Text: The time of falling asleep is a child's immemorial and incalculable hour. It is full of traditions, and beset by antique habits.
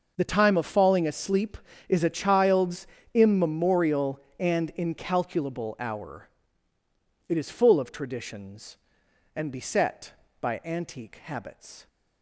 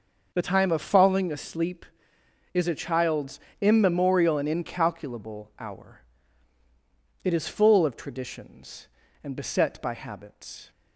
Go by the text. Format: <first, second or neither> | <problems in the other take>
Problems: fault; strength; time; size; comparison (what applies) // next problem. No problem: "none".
first | starts louder than the rest; until 1.3 s; 6 dB; noticeable in the first // pauses between "child's" and "immemorial"; slight; at 3.3 s; 0.20 s long; slight in the first // skips "antique"; at 9.9 s